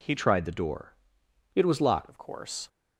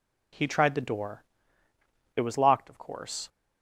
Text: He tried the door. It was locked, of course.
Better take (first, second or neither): second